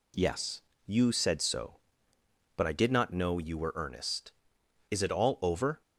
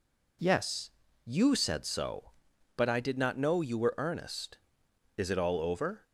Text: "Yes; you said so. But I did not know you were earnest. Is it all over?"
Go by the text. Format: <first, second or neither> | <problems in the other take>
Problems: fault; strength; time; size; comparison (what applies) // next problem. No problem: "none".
neither | none